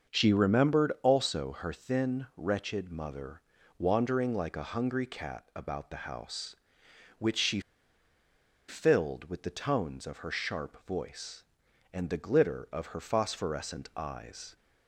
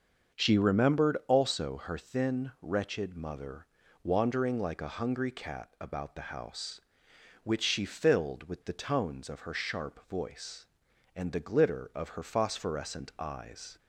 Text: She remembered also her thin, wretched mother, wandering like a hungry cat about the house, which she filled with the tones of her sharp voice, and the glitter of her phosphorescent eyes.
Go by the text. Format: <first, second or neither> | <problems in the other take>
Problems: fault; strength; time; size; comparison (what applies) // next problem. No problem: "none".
second | starts louder than the rest; until 1.1 s; 6.5 dB; also in the second // pauses between "she" and "filled"; at 7.5 s; 1.0 s long